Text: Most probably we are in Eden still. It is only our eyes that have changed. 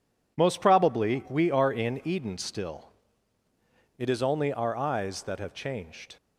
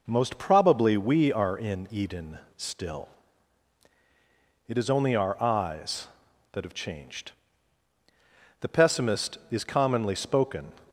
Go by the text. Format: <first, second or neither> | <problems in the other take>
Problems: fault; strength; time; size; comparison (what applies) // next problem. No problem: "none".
first | pauses between "Eden" and "still"; slight; at 2.3 s; 0.18 s long // goes on to say "The pessimist is commonly spoken"; strong; from 8.6 s on; 2.1 s long